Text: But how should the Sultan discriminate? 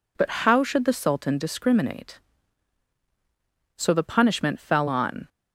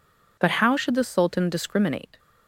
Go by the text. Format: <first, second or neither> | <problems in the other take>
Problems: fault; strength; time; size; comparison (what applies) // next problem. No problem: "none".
second | goes on to say "So the punishment fell on"; from 3.7 s on; 1.5 s long